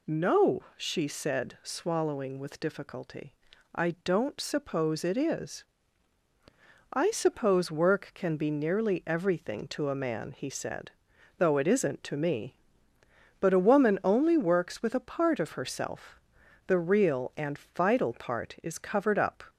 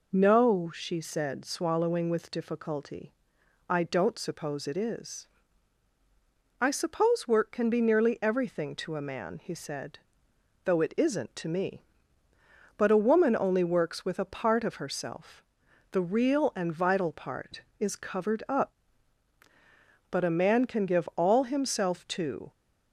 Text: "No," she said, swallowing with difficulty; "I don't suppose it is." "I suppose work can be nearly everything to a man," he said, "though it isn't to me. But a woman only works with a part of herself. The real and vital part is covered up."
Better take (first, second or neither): first